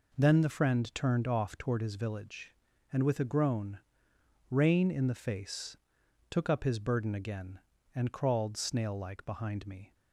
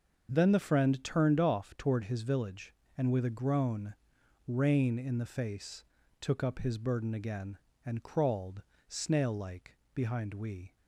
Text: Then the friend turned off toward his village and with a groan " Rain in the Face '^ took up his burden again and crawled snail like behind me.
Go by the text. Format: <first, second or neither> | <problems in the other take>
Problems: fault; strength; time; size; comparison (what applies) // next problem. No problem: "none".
first | starts louder than the rest; until 1.3 s; 6.5 dB // pauses between "crawled" and "snail"; slight; at 8.6 s; 0.26 s long // pauses between "like" and "behind"; slight; at 9.7 s; 0.20 s long // says "we" for "me"; at 10.3 s